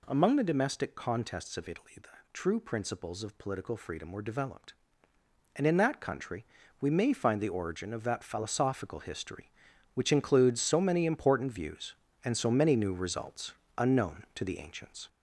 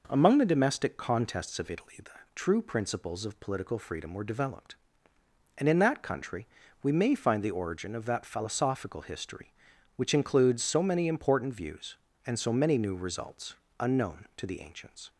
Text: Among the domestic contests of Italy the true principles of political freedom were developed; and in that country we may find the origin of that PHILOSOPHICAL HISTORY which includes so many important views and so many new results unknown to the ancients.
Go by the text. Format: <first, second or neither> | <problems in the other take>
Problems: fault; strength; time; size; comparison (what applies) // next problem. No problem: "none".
second | gets louder; throughout; 3.5 dB // pauses between "the" and "true"; slight; at 2.0 s; 0.24 s long; slight in the second // pauses between "country" and "we"; at 6.4 s; 0.38 s long; also in the second // pauses between "results" and "unknown"; slight; at 13.5 s; 0.24 s long; slight in the second